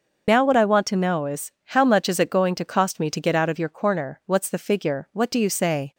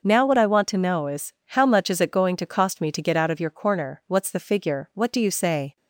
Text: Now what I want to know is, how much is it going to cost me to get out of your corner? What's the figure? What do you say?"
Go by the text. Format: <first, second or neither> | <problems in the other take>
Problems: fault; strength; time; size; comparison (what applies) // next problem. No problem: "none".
second | loses the start of "Now"; at 0.2 s; 55 ms // starts louder than the rest; until 1.2 s; 6 dB